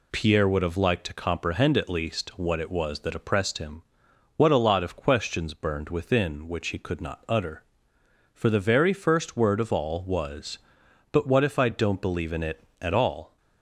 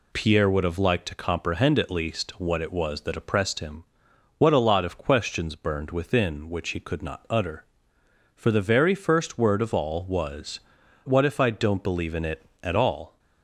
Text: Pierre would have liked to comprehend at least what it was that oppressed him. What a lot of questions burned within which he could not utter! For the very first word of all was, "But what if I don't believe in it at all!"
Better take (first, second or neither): first